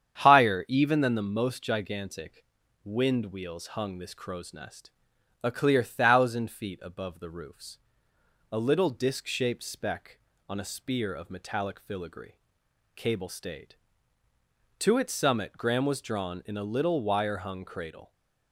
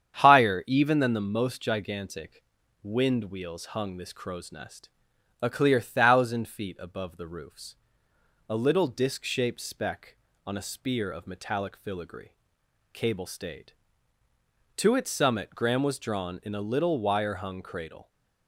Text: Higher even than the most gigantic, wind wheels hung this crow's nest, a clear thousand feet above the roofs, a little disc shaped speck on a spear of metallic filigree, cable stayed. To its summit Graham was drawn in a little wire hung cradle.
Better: neither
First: starts louder than the rest; strong; until 1.2 s; 8.5 dB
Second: starts louder than the rest; strong; until 1.2 s; 8.5 dB

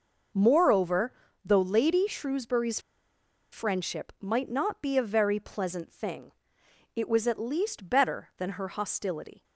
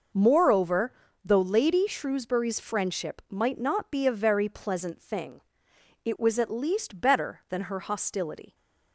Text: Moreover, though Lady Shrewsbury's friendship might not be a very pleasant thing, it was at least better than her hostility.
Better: second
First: pauses between "Shrewsbury's" and "friendship"; noticeable; at 2.8 s; 0.71 s long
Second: none

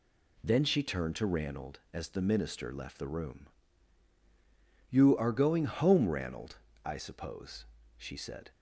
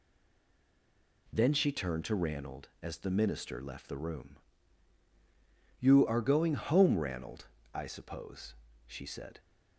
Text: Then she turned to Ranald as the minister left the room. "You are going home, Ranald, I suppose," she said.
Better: first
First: none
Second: stays silent before the first word; noticeable; until 1.2 s; 1.2 s long

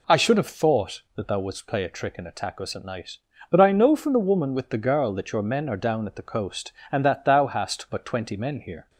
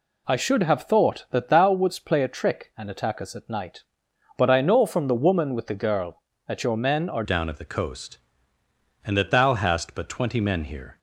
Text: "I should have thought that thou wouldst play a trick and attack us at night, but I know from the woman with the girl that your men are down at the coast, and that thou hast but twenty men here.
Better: first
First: none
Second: changes voice at "down"; from 7.2 s on; 3.7 s long

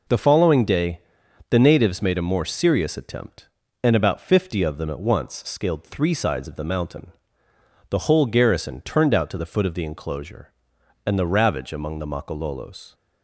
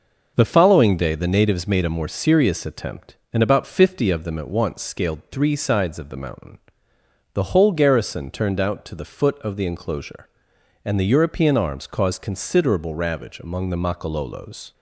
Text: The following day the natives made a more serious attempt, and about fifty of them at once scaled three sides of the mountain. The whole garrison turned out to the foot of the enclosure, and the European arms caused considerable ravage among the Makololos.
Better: second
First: pauses between "day" and "the"; noticeable; at 1.0 s; 0.48 s long // skips "European arms caused considerable"; at 11.2 s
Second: none

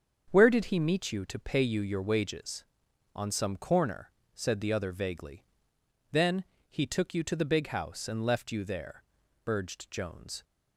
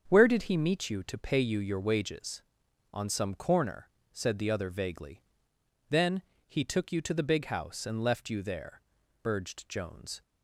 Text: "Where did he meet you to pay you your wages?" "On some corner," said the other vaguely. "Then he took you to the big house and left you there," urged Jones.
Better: neither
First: starts louder than the rest; until 1.3 s; 7 dB // pauses between "Then" and "he"; slight; at 6.4 s; 0.24 s long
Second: starts louder than the rest; strong; until 1.0 s; 7 dB // pauses between "Then" and "he"; slight; at 6.2 s; 0.24 s long

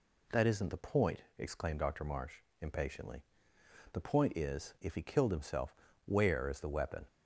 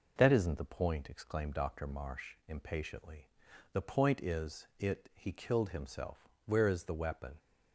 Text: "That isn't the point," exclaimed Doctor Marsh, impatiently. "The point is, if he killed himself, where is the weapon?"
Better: first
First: none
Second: says "it" for "if"; at 4.7 s

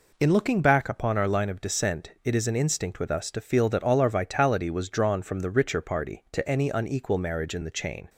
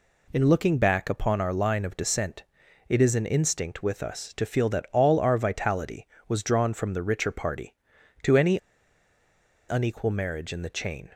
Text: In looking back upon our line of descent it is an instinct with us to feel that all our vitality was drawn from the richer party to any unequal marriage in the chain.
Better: first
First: none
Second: pauses between "descent" and "it"; at 2.4 s; 0.44 s long // pauses between "any" and "unequal"; at 8.5 s; 1.0 s long

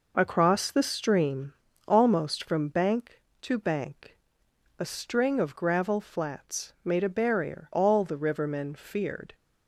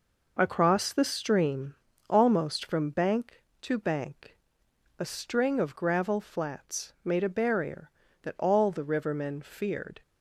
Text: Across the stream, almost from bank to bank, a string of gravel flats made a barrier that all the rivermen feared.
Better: second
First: skips "that"; at 7.7 s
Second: none

